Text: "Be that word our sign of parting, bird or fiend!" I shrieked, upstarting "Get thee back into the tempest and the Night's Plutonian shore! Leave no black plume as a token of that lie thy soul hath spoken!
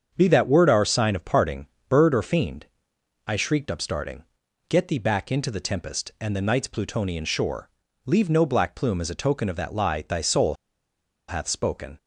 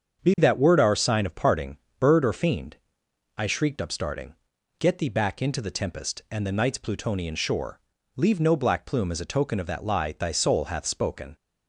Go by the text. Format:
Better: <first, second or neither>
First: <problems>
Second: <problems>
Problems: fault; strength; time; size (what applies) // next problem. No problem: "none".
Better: second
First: starts louder than the rest; strong; until 1.1 s; 7 dB // pauses between "upstarting" and "Get"; at 4.2 s; 0.44 s long // pauses between "soul" and "hath"; noticeable; at 10.5 s; 0.73 s long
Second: starts louder than the rest; strong; until 1.2 s; 7 dB // pauses between "upstarting" and "Get"; at 4.3 s; 0.44 s long